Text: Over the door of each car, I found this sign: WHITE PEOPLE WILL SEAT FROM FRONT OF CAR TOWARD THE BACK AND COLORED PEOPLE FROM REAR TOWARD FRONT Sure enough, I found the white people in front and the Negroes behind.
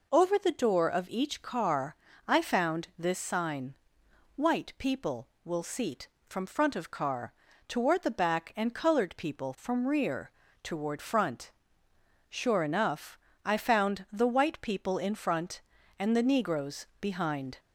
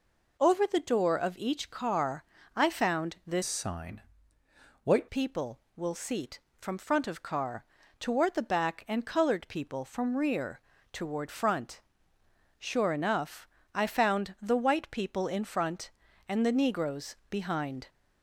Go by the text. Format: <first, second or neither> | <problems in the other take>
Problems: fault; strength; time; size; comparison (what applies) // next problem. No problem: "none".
first | changes voice from "sign" to "WHITE"; from 3.4 to 5.0 s; 1.6 s long // pauses between "CAR" and "TOWARD"; slight; at 7.6 s; 0.34 s long; slight in the first // pauses between "REAR" and "TOWARD"; slight; at 10.6 s; 0.32 s long; slight in the first // pauses between "FRONT" and "Sure"; noticeable; at 11.8 s; 0.78 s long; noticeable in the first // pauses between "Negroes" and "behind"; slight; at 17.1 s; 0.16 s long; slight in the first